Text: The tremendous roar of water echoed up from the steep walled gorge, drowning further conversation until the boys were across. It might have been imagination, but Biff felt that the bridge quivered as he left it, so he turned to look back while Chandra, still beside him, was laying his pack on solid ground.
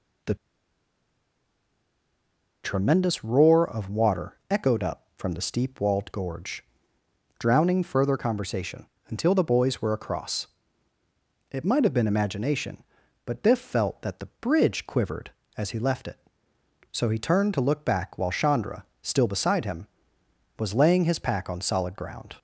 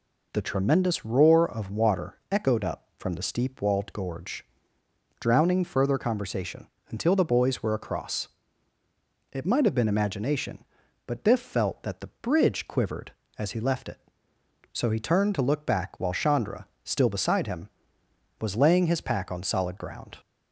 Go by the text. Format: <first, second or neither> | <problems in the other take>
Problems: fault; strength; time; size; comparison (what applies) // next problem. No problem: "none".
second | pauses between "The" and "tremendous"; strong; at 0.3 s; 2.2 s long // pauses between "conversation" and "until"; slight; at 8.8 s; 0.20 s long; slight in the second